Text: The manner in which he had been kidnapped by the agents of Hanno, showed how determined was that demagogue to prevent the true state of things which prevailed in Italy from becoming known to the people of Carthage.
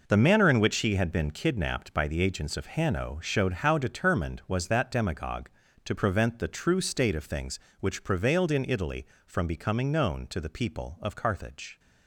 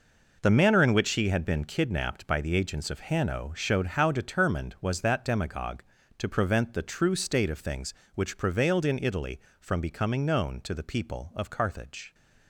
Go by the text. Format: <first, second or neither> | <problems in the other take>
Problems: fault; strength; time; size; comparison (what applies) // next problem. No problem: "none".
neither | none